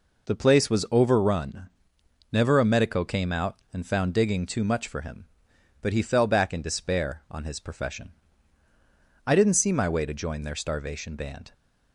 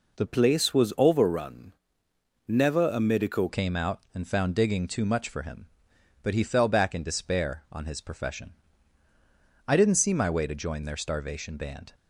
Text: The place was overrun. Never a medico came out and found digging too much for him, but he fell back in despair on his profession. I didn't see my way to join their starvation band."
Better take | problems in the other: first | changes voice from "place" to "medico"; from 0.2 to 3.4 s; 3.2 s long

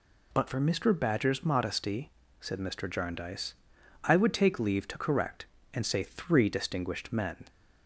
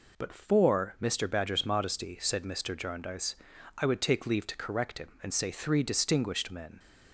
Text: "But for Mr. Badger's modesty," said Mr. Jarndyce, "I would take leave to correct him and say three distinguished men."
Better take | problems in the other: second | skips "him"; at 5.5 s

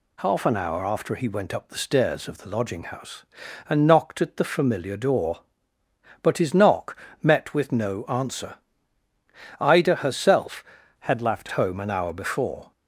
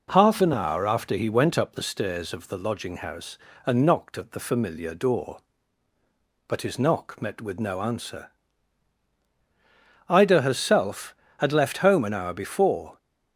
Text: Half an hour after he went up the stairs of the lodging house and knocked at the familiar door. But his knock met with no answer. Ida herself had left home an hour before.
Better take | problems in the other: second | pauses between "knock" and "met"; slight; at 6.9 s; 0.26 s long // changes voice from "had" to "left"; from 11.0 to 11.4 s; 0.4 s long

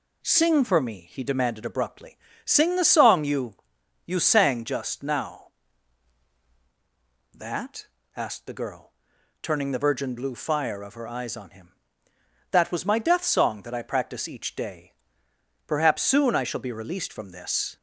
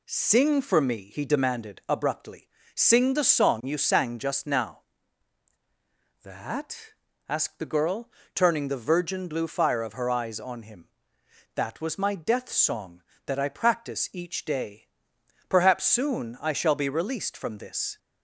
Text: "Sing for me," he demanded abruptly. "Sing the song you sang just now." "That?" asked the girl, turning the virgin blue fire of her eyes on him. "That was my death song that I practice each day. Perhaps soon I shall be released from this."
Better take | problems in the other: second | says "you" twice; at 4.0 s

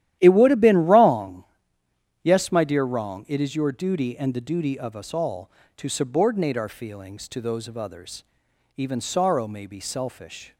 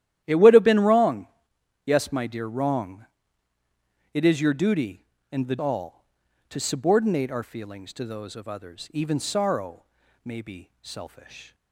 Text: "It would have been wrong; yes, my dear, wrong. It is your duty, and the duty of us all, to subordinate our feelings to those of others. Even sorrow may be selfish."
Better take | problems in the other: first | starts louder than the rest; strong; until 1.2 s; 12 dB; strong in the first // skips "duty of us"; at 5.5 s // pauses between "sorrow" and "may"; at 9.8 s; 0.40 s long

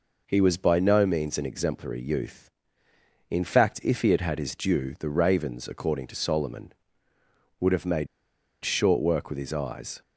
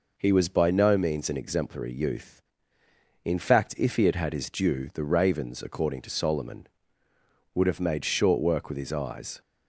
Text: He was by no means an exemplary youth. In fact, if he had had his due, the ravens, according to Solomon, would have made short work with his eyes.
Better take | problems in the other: second | pauses between "made" and "short"; noticeable; at 8.0 s; 0.58 s long

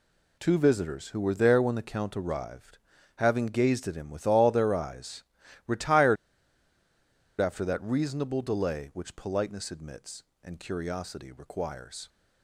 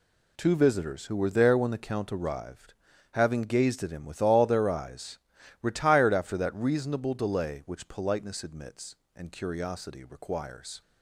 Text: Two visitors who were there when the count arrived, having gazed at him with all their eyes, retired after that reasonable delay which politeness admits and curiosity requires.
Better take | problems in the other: second | pauses between "retired" and "after"; at 6.1 s; 1.2 s long

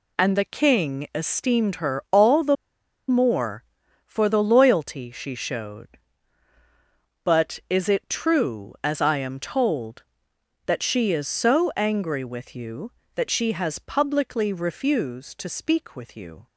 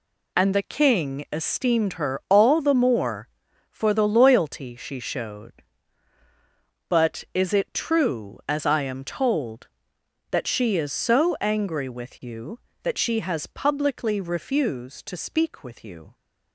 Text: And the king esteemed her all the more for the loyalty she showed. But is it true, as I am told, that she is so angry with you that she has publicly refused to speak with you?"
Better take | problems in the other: second | pauses between "the" and "more"; noticeable; at 2.5 s; 0.55 s long

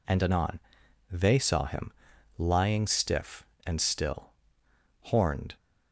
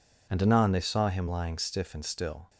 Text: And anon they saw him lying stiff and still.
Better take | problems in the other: second | pauses between "anon" and "they"; noticeable; at 0.5 s; 0.52 s long // pauses between "him" and "lying"; noticeable; at 1.9 s; 0.46 s long // goes on to say "Horned"; from 5.0 s on; 0.52 s long

